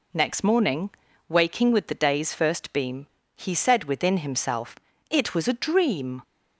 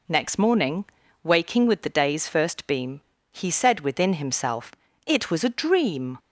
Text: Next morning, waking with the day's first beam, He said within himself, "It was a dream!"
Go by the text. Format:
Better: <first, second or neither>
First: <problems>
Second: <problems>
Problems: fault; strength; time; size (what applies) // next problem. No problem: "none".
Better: neither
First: none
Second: none